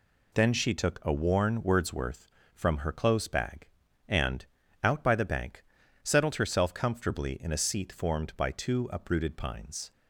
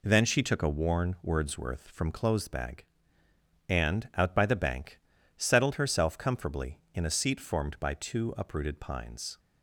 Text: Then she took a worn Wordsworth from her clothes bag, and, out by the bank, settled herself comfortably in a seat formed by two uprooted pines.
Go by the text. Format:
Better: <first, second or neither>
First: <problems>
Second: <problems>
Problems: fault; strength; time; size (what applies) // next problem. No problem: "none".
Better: first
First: none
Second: skips "her"; at 2.1 s